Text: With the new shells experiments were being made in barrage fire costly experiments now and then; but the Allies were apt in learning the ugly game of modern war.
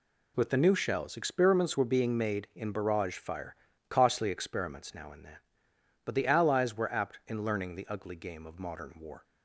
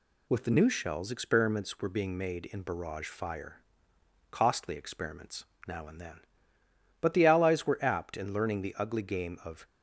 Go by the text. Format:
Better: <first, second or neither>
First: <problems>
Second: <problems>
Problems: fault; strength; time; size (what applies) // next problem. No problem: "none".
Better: first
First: pauses between "fire" and "costly"; slight; at 3.5 s; 0.32 s long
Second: pauses between "fire" and "costly"; noticeable; at 3.6 s; 0.68 s long // pauses between "experiments" and "now"; slight; at 5.4 s; 0.24 s long // stops before "modern war"; at 9.6 s